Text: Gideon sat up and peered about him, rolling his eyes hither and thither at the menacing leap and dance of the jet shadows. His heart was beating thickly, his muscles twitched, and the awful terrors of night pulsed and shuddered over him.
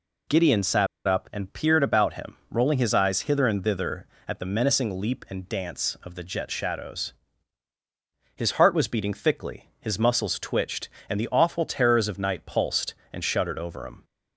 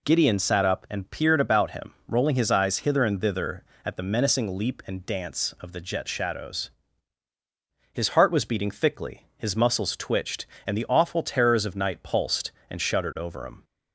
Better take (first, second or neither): second